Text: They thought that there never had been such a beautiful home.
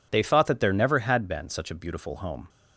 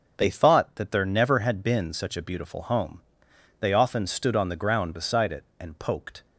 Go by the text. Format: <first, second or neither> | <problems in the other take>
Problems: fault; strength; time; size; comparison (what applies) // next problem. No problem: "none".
first | goes on to say "They often stood on the ground beside it and poked"; strong; from 3.5 s on; 2.6 s long